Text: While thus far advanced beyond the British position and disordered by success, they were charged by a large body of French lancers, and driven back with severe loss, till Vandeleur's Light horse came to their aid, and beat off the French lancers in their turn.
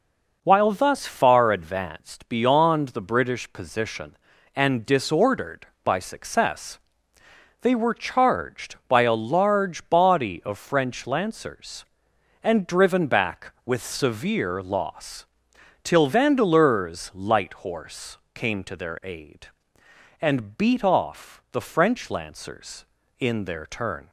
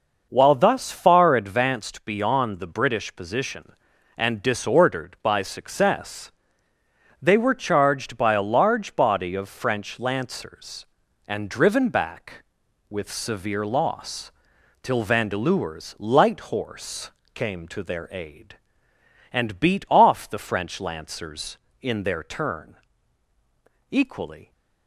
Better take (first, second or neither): first